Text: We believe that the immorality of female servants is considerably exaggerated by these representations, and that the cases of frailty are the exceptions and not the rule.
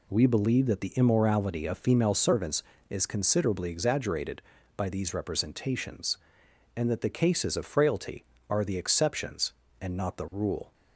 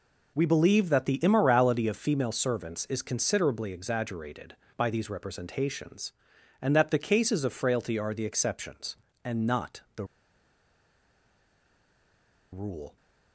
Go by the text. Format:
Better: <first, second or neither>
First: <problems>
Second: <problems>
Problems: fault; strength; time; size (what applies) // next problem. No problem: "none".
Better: first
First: none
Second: pauses between "the" and "rule"; strong; at 10.0 s; 2.4 s long